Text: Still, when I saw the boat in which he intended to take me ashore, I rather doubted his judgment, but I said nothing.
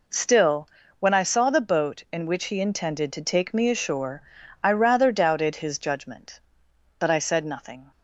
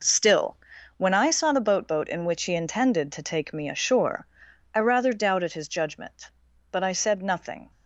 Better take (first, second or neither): first